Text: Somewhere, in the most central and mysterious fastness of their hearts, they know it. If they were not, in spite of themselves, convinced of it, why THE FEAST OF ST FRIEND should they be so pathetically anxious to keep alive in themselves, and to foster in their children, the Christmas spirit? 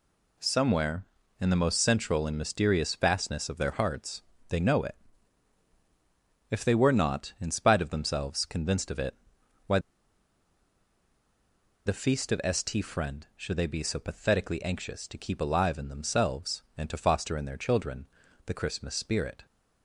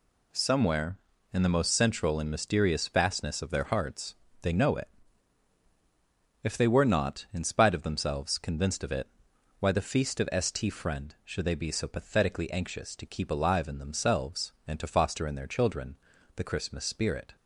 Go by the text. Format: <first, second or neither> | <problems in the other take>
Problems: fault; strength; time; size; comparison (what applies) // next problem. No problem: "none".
second | pauses between "why" and "THE"; strong; at 9.7 s; 2.0 s long